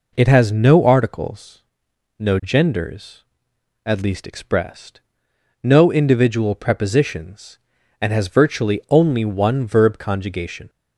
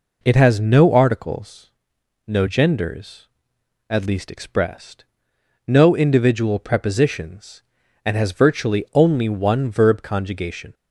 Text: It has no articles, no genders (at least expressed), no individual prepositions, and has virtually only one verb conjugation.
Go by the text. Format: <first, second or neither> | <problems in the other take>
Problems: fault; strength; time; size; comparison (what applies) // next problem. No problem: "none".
neither | none